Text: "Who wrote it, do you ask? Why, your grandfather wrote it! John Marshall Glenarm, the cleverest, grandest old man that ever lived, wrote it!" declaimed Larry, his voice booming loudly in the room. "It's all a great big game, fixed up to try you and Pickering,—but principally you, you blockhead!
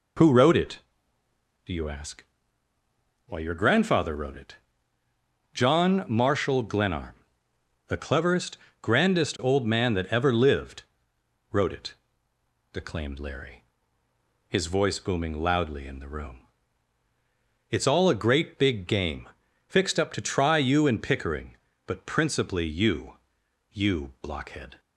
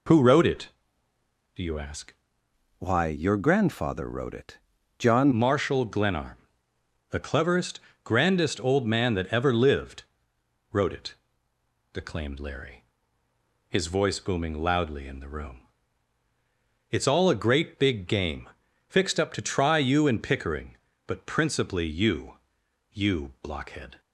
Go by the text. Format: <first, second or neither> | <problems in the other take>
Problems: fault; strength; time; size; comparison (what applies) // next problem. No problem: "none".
first | changes voice from "Why" to "John"; from 2.7 to 5.2 s; 2.5 s long